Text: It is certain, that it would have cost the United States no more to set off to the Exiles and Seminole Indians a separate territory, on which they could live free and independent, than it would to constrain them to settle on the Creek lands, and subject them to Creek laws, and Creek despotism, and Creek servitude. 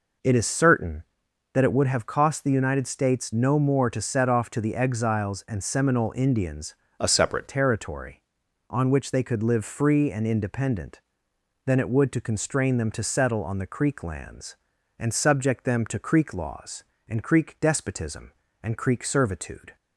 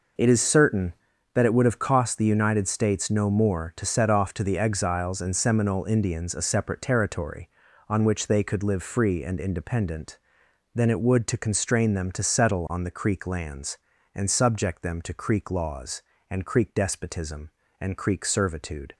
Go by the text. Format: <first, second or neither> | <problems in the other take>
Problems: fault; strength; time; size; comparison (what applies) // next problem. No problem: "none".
second | changes voice from "a" to "separate"; from 7.0 to 7.4 s; 0.4 s long